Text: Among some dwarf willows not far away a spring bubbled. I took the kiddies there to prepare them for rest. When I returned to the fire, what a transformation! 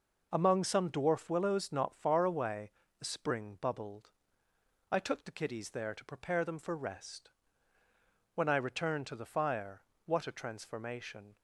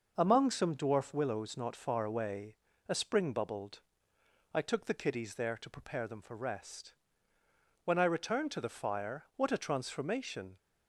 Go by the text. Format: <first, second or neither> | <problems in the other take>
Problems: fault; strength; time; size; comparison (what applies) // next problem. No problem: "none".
neither | pauses between "away" and "a"; slight; the same in both